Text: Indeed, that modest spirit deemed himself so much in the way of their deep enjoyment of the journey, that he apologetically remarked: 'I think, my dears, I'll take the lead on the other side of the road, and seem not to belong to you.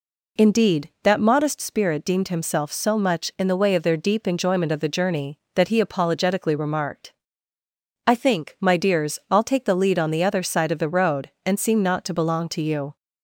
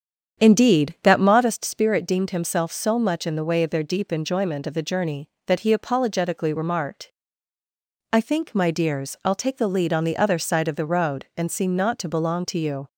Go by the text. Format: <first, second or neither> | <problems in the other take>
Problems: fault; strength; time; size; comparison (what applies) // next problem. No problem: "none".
first | starts louder than the rest; strong; until 1.5 s; 8 dB